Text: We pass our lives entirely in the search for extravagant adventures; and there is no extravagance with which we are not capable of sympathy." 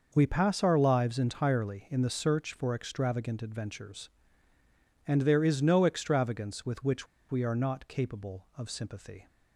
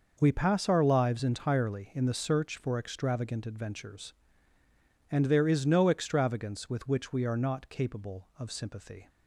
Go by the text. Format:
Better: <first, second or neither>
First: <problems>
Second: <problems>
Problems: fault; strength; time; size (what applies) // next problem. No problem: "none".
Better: second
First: pauses between "which" and "we"; slight; at 7.0 s; 0.24 s long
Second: none